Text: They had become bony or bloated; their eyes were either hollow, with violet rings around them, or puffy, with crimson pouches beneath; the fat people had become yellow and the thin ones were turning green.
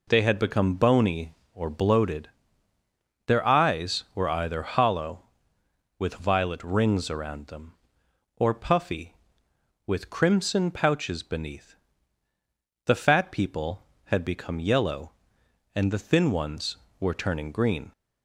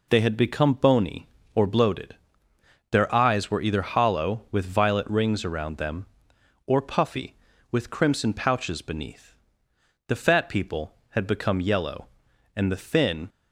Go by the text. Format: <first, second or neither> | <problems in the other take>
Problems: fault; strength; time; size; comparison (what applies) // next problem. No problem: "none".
first | stops before "ones were turning green"; at 13.2 s